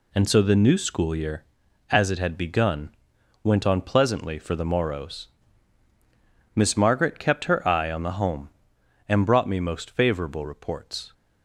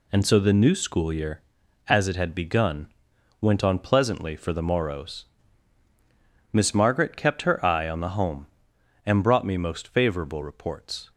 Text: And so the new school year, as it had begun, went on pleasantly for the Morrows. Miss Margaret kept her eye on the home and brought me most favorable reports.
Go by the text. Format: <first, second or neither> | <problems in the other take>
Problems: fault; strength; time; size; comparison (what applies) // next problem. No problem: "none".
neither | none